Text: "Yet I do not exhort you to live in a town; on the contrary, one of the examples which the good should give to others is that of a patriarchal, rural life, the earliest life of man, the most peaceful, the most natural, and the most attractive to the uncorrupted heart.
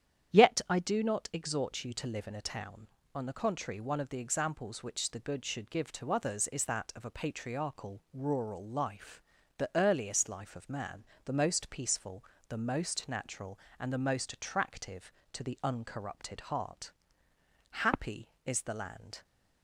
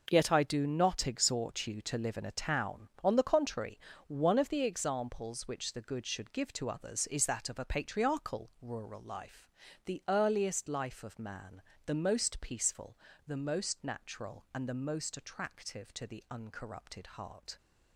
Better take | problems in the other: second | starts louder than the rest; strong; until 1.4 s; 9.5 dB // goes on to say "Happy is the land"; from 17.7 s on; 1.5 s long

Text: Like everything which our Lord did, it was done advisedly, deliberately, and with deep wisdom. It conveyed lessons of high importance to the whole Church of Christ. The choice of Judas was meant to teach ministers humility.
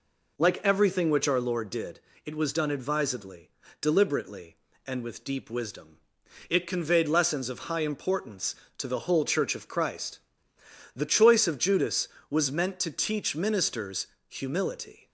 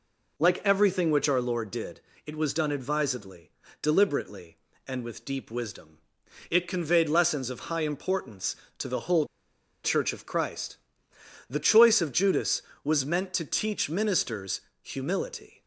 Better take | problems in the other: first | pauses between "whole" and "Church"; noticeable; at 9.2 s; 0.59 s long // pauses between "ministers" and "humility"; slight; at 14.5 s; 0.24 s long; slight in the first

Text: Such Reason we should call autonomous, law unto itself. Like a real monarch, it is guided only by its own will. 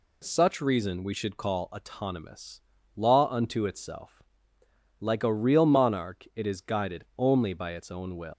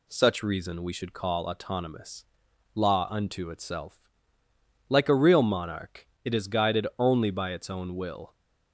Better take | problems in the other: second | pauses between "guided" and "only"; slight; at 7.0 s; 0.16 s long // leaves "will" unfinished; at 8.3 s; 130 ms

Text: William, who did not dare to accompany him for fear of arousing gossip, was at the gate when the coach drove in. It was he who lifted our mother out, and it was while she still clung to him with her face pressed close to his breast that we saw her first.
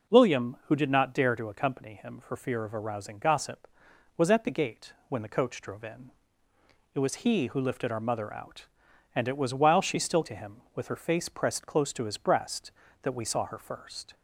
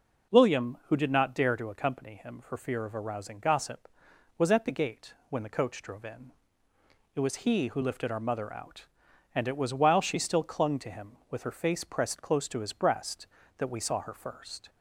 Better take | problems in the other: second | pauses between "gate" and "when"; slight; at 4.9 s; 0.16 s long; slight in the second // skips "clung"; at 10.2 s

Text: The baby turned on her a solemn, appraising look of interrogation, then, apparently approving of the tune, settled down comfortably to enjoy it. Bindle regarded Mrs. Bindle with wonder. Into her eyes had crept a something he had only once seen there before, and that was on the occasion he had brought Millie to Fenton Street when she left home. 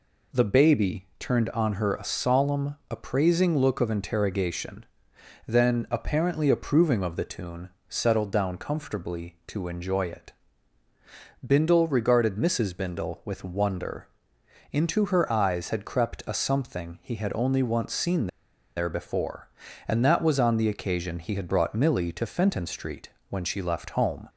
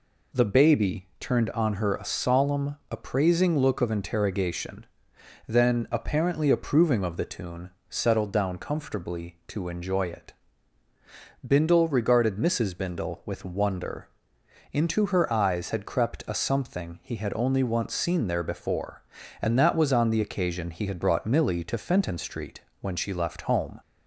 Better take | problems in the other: second | pauses between "seen" and "there"; noticeable; at 18.2 s; 0.49 s long // pauses between "Street" and "when"; slight; at 23.0 s; 0.20 s long; slight in the second

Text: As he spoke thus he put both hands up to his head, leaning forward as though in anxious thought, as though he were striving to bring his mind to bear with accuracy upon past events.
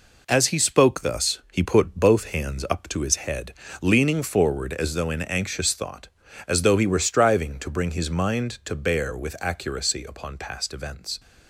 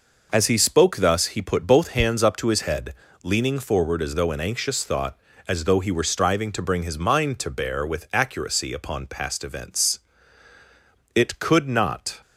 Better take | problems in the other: first | goes on to say "It could not"; noticeable; from 11.1 s on; 1.0 s long

